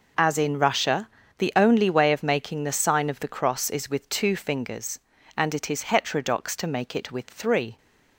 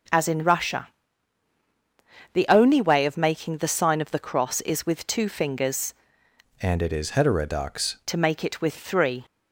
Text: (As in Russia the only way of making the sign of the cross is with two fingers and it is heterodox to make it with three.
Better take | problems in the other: first | starts louder than the rest; until 2.6 s; 6.5 dB // pauses between "Russia" and "the"; strong; at 0.8 s; 1.4 s long; slight in the first // changes voice from "and" to "heterodox"; from 6.6 to 7.9 s; 1.3 s long

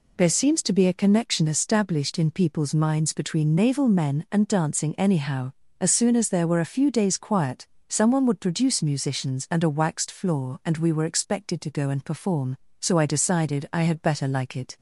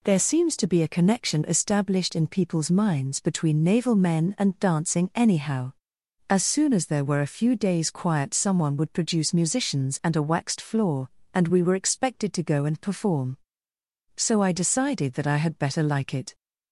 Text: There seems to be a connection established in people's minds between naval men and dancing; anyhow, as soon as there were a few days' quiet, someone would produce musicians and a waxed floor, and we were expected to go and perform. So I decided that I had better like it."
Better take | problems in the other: second | skips "that"; at 13.6 s

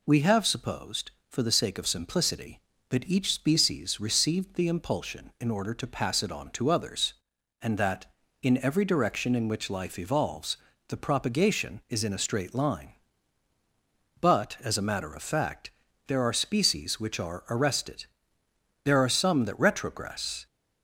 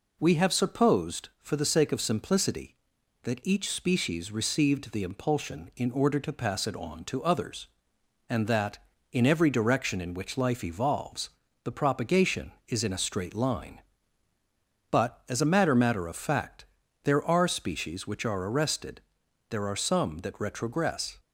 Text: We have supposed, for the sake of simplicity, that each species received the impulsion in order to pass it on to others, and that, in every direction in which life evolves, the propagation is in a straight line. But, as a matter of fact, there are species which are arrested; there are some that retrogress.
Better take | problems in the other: first | says "matter" twice; at 15.7 s

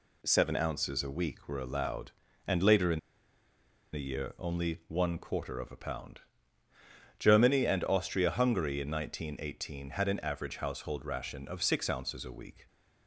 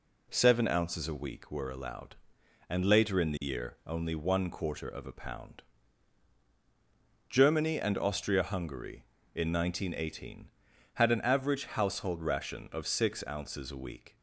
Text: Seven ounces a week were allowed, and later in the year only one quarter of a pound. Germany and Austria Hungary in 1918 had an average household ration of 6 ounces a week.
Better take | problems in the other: second | pauses between "in" and "the"; noticeable; at 2.9 s; 0.93 s long

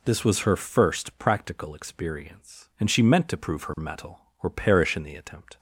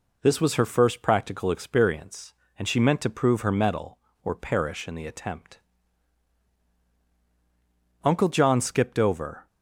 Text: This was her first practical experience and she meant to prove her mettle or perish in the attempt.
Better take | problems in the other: first | goes on to say "Uncle John skipped over"; from 8.0 s on; 1.4 s long

